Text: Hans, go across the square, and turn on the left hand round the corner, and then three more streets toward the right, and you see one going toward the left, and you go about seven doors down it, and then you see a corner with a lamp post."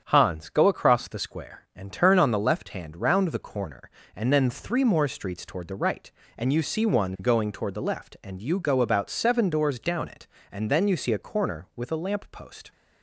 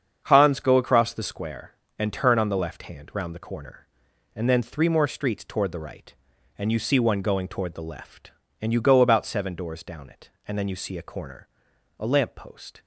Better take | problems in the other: first | starts louder than the rest; strong; until 1.2 s; 7.5 dB; strong in the first // skips "with"; at 11.7 s

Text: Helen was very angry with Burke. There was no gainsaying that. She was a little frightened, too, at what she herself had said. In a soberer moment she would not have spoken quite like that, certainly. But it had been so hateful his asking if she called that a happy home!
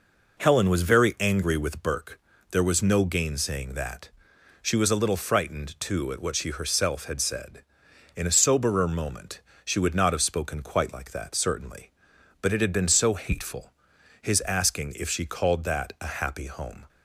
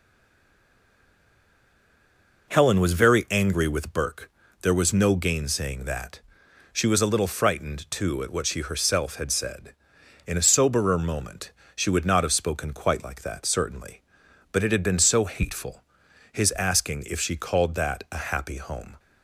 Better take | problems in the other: first | stays silent before the first word; until 2.4 s; 2.4 s long // pauses between "moment" and "she"; slight; at 11.5 s; 0.24 s long; slight in the first // pauses between "hateful" and "his"; noticeable; at 15.8 s; 0.50 s long; noticeable in the first

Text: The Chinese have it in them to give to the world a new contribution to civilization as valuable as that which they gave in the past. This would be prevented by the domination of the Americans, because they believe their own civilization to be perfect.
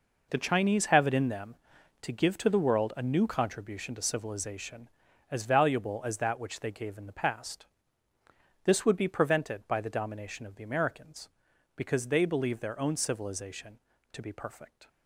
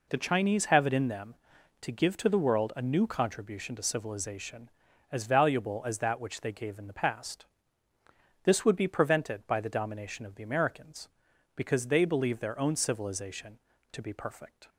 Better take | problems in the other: second | gets quieter; strong; throughout; 12 dB

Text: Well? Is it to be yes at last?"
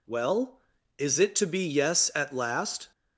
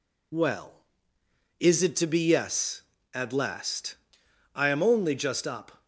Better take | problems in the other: first | goes on to say "I am only just up"; noticeable; from 4.5 s on; 1.3 s long

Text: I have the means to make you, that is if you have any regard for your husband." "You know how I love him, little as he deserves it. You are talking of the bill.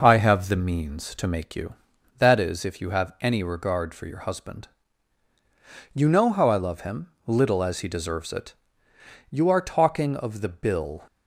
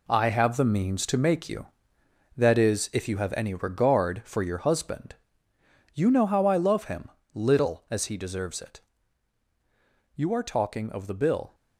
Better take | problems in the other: first | gets quieter; strong; throughout; 9 dB

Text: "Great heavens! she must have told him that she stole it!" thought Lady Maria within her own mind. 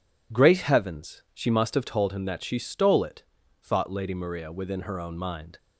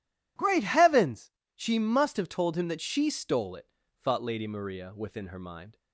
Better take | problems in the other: first | skips "own"; at 5.3 s

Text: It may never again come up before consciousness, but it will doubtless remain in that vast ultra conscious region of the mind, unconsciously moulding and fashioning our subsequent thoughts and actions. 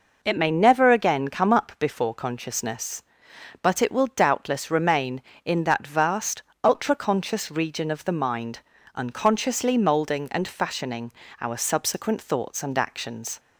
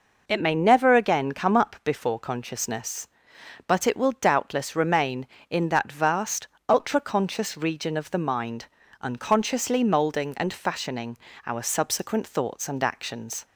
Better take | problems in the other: neither | pauses between "vast" and "ultra"; slight; the same in both // pauses between "fashioning" and "our"; slight; the same in both

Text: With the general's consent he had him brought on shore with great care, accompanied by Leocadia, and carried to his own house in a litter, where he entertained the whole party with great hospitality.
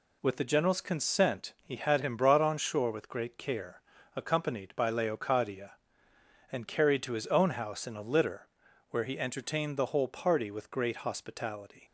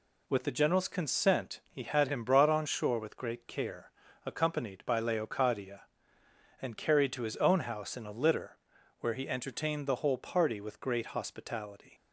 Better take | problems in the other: neither | none

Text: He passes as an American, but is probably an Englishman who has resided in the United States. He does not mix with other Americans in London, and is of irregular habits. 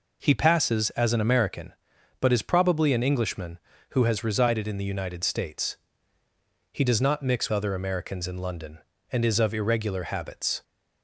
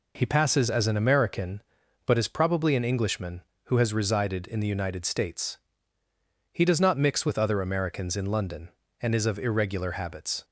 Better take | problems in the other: second | skips "with"; at 7.5 s

